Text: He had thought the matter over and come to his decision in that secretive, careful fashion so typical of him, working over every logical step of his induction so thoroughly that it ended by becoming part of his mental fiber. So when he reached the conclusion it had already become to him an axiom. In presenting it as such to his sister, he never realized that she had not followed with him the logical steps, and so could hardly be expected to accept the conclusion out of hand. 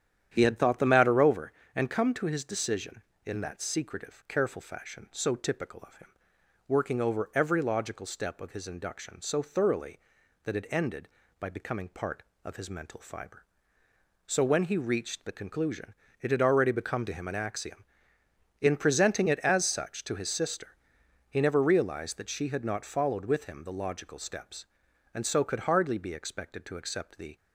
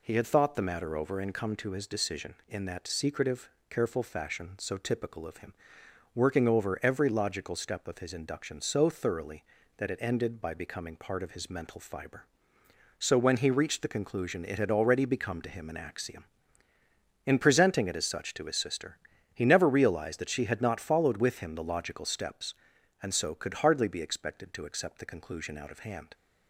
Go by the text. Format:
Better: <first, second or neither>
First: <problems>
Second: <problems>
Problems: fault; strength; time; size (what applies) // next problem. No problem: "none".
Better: second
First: starts louder than the rest; strong; until 1.3 s; 10 dB // pauses between "conclusion" and "it"; slight; at 15.9 s; 0.30 s long // stops before "conclusion out of hand"; at 27.3 s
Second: none